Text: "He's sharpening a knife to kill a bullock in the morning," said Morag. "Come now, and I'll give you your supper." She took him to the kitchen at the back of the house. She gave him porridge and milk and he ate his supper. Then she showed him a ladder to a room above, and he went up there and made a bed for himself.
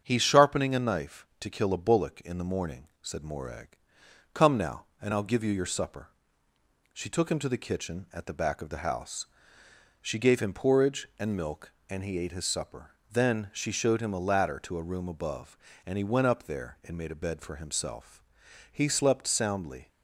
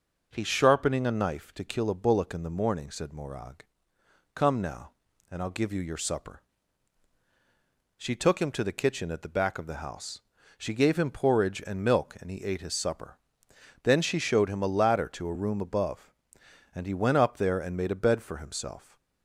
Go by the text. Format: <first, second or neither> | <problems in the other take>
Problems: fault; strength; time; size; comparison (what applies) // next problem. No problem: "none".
second | starts louder than the rest; strong; until 1.0 s; 8 dB // goes on to say "He slept soundly"; noticeable; from 18.7 s on; 1.1 s long